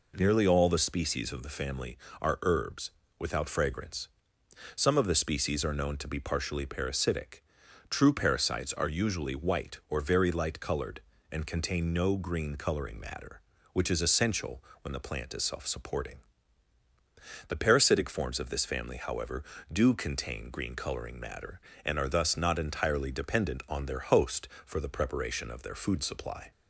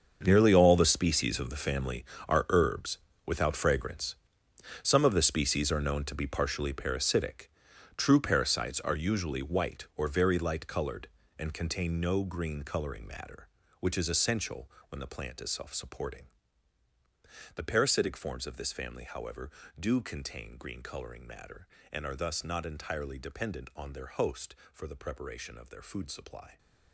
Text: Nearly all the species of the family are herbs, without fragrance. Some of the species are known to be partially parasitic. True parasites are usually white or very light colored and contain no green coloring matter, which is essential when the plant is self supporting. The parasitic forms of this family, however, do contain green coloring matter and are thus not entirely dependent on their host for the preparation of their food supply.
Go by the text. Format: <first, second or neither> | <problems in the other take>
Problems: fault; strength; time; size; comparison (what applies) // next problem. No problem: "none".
first | gets quieter; strong; throughout; 14.5 dB // pauses between "essential" and "when"; slight; at 14.6 s; 0.20 s long; slight in the first